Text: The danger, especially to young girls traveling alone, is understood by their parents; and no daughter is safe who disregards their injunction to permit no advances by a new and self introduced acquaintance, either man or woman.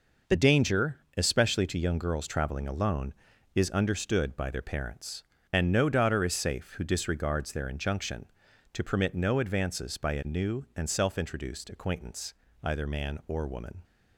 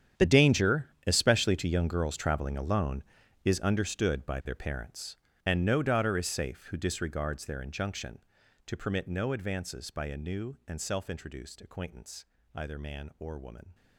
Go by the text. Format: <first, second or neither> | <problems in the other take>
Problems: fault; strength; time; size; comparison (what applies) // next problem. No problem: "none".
first | gets quieter; strong; throughout; 16.5 dB